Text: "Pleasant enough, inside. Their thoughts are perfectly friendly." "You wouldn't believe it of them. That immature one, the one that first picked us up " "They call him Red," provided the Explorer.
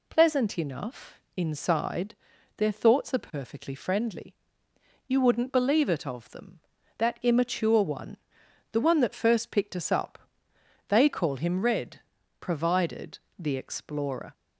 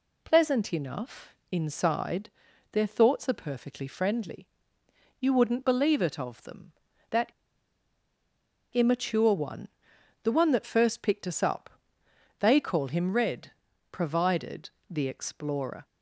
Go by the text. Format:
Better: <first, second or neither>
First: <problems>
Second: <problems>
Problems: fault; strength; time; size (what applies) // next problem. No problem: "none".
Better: first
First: pauses between "provided" and "the"; slight; at 13.1 s; 0.18 s long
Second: pauses between "That" and "immature"; strong; at 7.3 s; 1.4 s long // pauses between "provided" and "the"; slight; at 14.7 s; 0.18 s long